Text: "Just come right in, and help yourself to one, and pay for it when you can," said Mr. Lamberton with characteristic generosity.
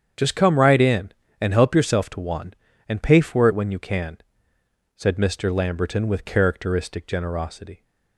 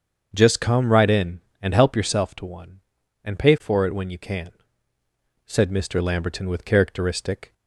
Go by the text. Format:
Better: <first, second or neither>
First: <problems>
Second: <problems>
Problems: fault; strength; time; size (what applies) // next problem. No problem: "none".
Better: first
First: starts louder than the rest; strong; until 1.4 s; 7.5 dB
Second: starts louder than the rest; until 1.3 s; 7 dB // stops before "generosity"; at 7.5 s